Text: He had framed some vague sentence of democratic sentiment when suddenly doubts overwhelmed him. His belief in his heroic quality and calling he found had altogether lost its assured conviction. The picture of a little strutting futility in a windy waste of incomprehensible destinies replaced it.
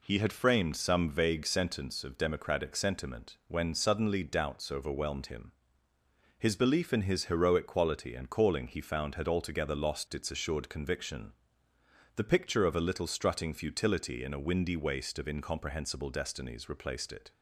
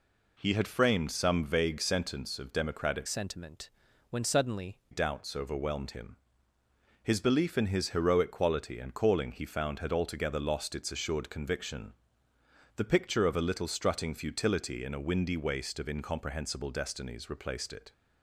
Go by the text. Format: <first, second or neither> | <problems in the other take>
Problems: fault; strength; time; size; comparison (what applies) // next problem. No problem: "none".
first | changes voice from "sentiment" to "suddenly"; from 3.0 to 4.7 s; 1.7 s long // pauses between "sentiment" and "when"; at 3.7 s; 0.40 s long